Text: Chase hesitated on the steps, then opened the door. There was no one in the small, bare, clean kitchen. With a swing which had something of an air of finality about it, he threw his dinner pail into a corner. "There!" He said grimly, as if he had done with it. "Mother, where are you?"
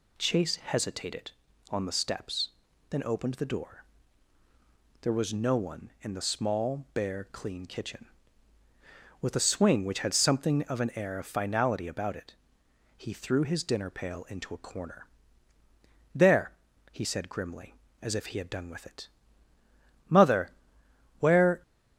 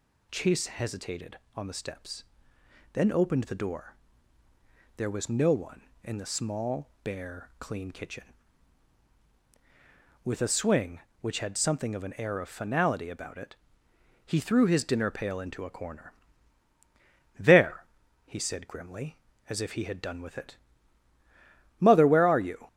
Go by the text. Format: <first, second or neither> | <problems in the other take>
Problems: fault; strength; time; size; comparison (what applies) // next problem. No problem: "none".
second | stops before "are you"; at 21.6 s